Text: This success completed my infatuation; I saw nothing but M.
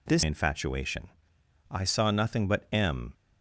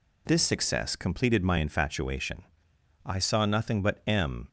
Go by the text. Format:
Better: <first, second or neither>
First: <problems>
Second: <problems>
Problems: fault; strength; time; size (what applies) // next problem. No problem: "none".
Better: second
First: skips "success completed my"; at 0.2 s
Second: none